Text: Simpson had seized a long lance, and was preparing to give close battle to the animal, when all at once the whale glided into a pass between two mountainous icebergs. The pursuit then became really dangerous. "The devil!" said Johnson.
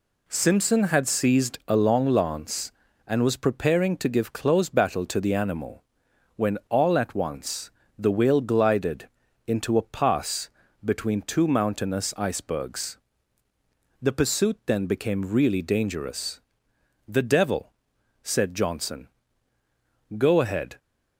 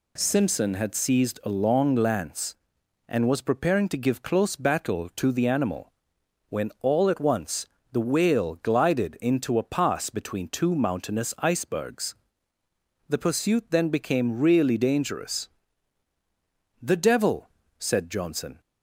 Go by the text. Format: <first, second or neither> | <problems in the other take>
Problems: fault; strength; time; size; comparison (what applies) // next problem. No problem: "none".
second | pauses between "once" and "the"; slight; at 7.7 s; 0.26 s long; slight in the second // pauses between "glided" and "into"; at 9.0 s; 0.38 s long // pauses between "pass" and "between"; slight; at 10.5 s; 0.34 s long // goes on to say "Go ahead"; noticeable; from 20.1 s on; 0.62 s long